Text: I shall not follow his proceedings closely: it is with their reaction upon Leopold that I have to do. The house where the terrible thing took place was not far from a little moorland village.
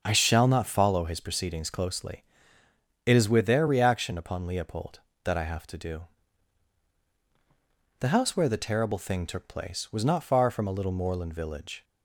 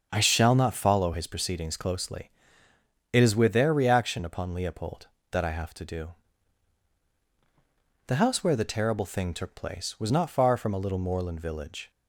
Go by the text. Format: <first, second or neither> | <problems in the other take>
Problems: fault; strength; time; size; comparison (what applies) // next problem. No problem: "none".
neither | starts louder than the rest; the same in both